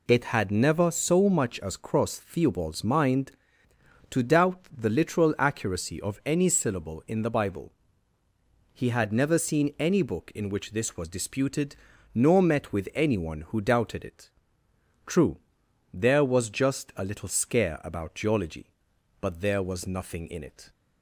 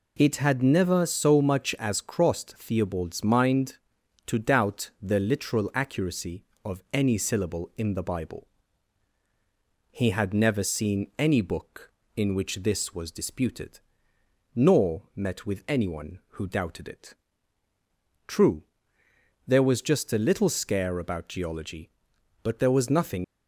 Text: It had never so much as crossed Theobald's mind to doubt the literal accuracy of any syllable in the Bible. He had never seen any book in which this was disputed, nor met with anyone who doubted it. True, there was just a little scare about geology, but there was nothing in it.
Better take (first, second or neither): first